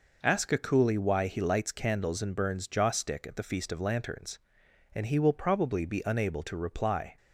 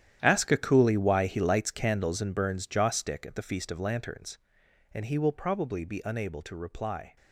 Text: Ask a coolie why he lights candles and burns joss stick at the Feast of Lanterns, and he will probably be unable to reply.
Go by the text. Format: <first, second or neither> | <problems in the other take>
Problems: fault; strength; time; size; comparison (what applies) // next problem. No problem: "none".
first | gets quieter; strong; throughout; 14 dB